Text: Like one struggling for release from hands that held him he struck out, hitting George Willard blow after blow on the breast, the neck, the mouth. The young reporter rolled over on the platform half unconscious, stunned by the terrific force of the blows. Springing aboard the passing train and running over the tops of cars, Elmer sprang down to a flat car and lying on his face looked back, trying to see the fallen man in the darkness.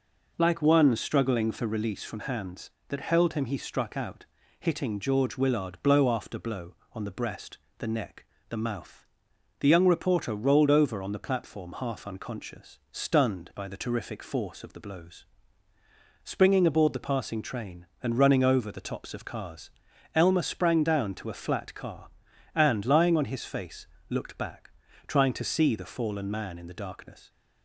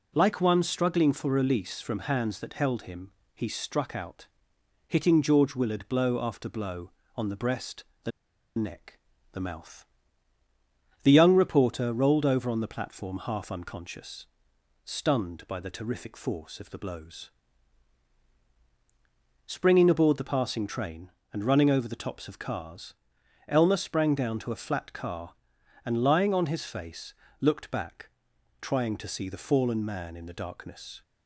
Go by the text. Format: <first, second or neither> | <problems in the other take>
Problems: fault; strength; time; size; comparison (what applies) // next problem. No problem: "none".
first | pauses between "him" and "he"; slight; at 3.1 s; 0.20 s long // pauses between "the" and "neck"; noticeable; at 8.1 s; 0.47 s long // pauses between "face" and "looked"; slight; at 27.1 s; 0.26 s long; slight in the first